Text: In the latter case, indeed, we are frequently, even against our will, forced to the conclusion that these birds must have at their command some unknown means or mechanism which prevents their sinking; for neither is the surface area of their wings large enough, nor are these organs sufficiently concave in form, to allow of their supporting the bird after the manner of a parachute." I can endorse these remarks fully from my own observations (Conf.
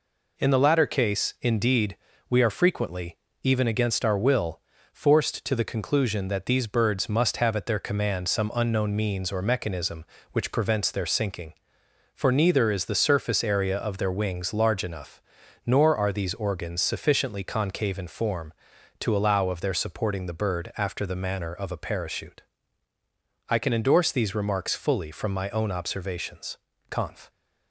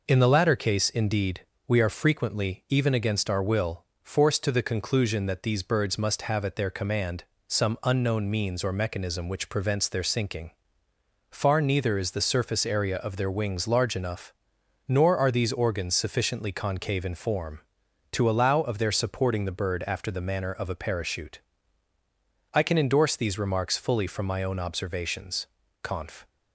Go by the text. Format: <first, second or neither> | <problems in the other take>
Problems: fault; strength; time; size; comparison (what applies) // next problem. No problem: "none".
first | pauses between "command" and "some"; slight; at 7.2 s; 0.24 s long // says "far" for "for"; at 11.3 s